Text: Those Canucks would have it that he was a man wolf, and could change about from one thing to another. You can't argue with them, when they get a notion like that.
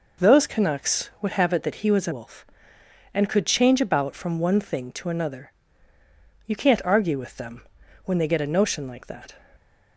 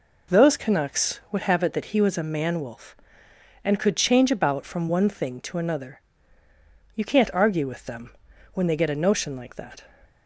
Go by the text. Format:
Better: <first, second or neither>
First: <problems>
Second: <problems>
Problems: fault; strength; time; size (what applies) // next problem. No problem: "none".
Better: second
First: skips "man"; at 2.1 s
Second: none